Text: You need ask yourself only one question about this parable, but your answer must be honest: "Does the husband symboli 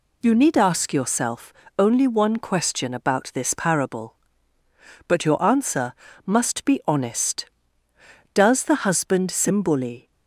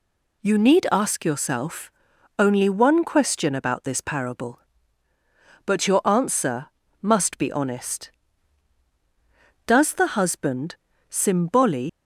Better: first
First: pauses between "yourself" and "only"; slight; at 1.5 s; 0.28 s long // pauses between "answer" and "must"; slight; at 5.9 s; 0.32 s long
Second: pauses between "yourself" and "only"; noticeable; at 1.9 s; 0.46 s long // pauses between "answer" and "must"; slight; at 6.6 s; 0.34 s long // pauses between "husband" and "symboli"; slight; at 10.7 s; 0.34 s long // leaves "symboli" unfinished; at 11.8 s; 80 ms

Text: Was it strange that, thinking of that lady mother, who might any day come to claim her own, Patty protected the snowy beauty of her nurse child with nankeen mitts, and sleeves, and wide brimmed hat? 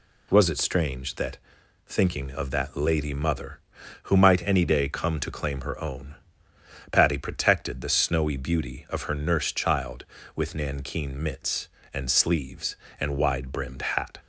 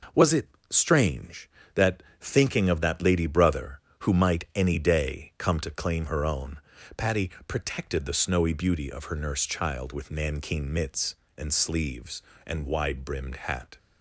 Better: first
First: none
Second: pauses between "it" and "strange"; slight; at 0.4 s; 0.22 s long // says "brother" for "mother"; at 3.2 s // pauses between "Patty" and "protected"; slight; at 7.2 s; 0.18 s long

